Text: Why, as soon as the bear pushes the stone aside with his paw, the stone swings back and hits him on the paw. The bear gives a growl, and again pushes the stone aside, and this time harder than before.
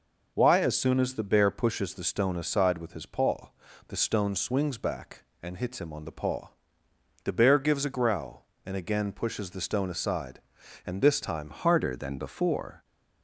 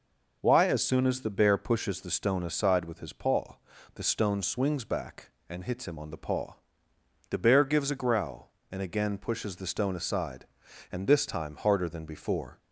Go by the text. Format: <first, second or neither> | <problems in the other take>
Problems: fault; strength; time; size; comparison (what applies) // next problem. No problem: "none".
second | changes voice at "harder"; from 11.5 s on; 1.3 s long